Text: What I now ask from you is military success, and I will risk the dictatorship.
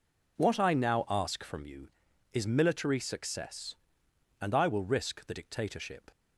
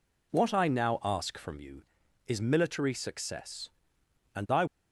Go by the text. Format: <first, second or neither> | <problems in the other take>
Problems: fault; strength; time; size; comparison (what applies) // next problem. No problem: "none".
first | stops before "will risk the dictatorship"; at 4.6 s